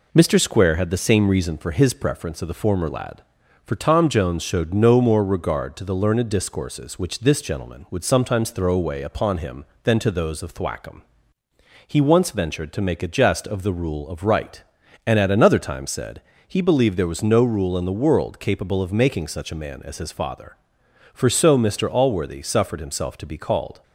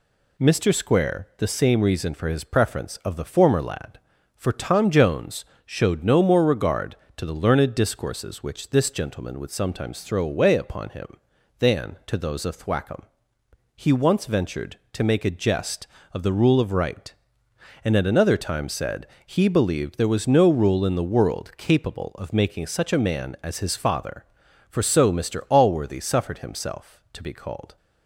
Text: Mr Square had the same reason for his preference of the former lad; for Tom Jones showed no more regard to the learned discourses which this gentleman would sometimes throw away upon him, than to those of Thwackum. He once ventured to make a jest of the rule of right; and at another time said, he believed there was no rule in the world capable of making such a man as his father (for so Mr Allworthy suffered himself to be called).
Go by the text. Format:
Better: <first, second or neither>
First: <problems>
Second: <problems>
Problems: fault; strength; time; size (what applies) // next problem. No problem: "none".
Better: first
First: none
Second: skips "had"; at 1.3 s // pauses between "Jones" and "showed"; slight; at 5.4 s; 0.20 s long